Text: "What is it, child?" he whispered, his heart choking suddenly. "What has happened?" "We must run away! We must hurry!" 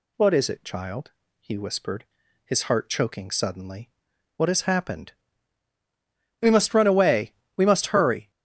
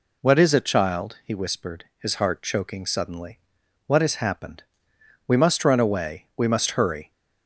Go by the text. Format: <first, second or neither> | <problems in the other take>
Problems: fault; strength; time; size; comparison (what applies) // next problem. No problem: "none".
neither | none